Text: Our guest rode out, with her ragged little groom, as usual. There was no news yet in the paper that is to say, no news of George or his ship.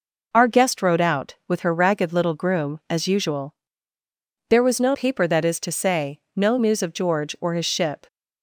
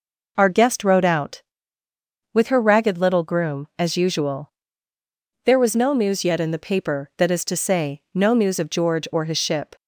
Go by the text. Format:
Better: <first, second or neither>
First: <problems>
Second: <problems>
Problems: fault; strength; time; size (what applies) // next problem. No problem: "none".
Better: second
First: skips "news yet in the"; at 4.9 s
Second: none